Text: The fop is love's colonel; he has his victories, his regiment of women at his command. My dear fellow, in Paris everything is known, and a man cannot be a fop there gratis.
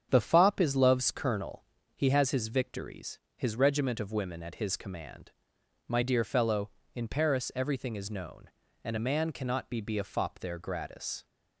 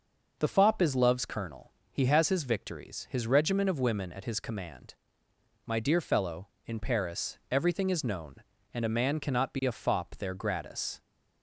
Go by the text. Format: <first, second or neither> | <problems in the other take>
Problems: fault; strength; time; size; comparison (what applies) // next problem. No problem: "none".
second | starts louder than the rest; strong; until 1.1 s; 8 dB // says "be" twice; at 9.8 s